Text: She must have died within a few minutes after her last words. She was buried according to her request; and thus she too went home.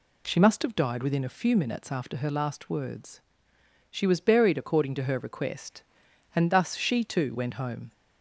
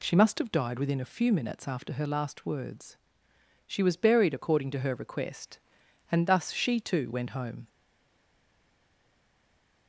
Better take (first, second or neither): first